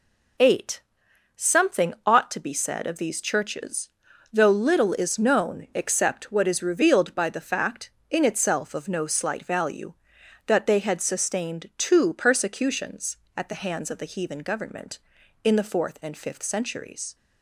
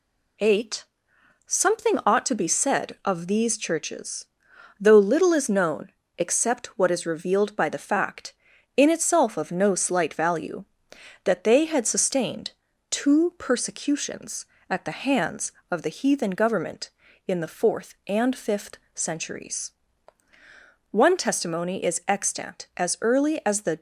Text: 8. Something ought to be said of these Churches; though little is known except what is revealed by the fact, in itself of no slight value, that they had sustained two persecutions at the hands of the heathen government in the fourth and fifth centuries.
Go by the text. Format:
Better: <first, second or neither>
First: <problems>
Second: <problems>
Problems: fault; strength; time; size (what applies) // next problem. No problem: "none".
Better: first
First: none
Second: pauses between "known" and "except"; slight; at 5.9 s; 0.26 s long // pauses between "sustained" and "two"; at 12.5 s; 0.38 s long // pauses between "fifth" and "centuries"; slight; at 18.7 s; 0.18 s long // goes on to say "One testimony is extant as early as the"; strong; from 20.8 s on; 2.9 s long